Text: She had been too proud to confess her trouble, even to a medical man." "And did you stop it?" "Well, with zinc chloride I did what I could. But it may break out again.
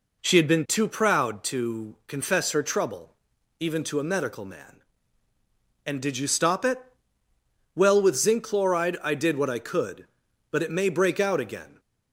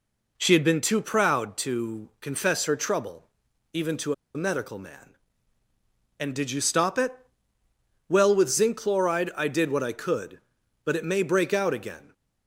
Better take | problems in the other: first | pauses between "to" and "a"; slight; at 4.1 s; 0.21 s long

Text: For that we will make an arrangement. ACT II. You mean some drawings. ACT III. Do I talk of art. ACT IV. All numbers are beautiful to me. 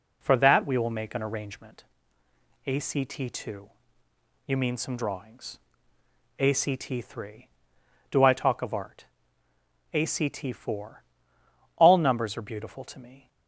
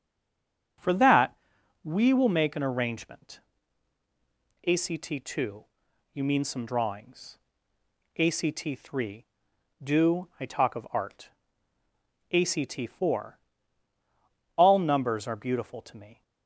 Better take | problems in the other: first | stays silent before the first word; slight; until 0.7 s; 0.7 s long // starts louder than the rest; until 2.2 s; 7 dB // pauses between "that" and "we"; noticeable; at 1.3 s; 0.48 s long

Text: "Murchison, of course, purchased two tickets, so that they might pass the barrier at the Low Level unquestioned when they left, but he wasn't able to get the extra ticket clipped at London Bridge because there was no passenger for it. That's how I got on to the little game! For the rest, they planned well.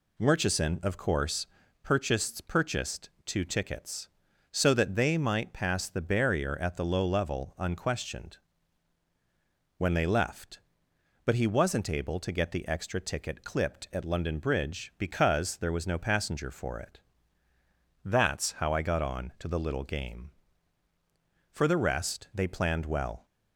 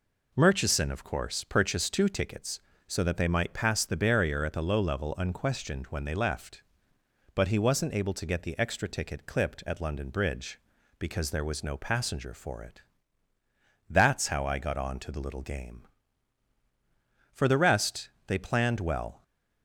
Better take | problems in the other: second | says "purchased" twice; at 2.4 s // pauses between "unquestioned" and "when"; strong; at 8.3 s; 1.4 s long

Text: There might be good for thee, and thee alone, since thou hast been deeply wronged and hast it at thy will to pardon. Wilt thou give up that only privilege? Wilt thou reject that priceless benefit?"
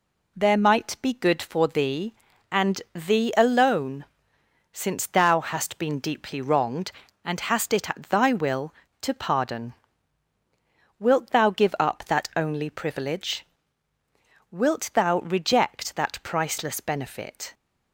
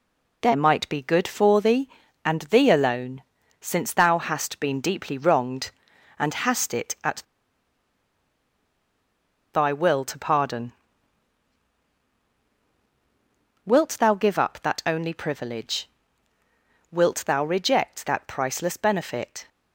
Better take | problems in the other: first | pauses between "at" and "thy"; strong; at 7.2 s; 2.3 s long

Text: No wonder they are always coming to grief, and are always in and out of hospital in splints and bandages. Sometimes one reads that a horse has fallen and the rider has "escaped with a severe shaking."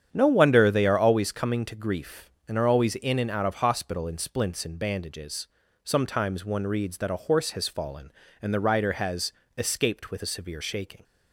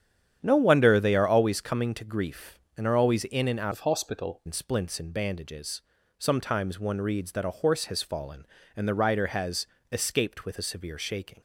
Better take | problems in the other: first | starts louder than the rest; strong; until 1.4 s; 9 dB; strong in the first // changes voice from "of" to "hospital"; from 3.7 to 4.4 s; 0.7 s long // pauses between "has" and "escaped"; slight; at 9.6 s; 0.26 s long; slight in the first

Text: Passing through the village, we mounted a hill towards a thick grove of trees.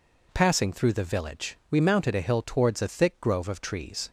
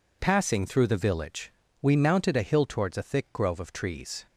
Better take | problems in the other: neither | none

